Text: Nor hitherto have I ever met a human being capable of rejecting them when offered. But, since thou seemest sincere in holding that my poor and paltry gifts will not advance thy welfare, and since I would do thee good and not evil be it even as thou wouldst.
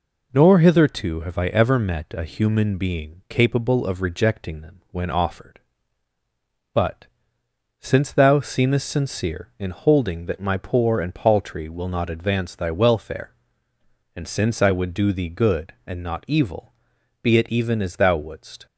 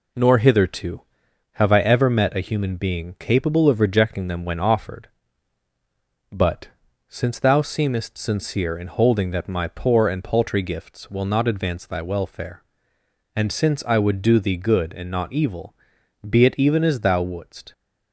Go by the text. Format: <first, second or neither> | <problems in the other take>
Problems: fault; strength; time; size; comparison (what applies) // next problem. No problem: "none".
second | skips "gifts"; at 11.6 s // pauses between "evil" and "be"; noticeable; at 16.7 s; 0.48 s long; noticeable in the second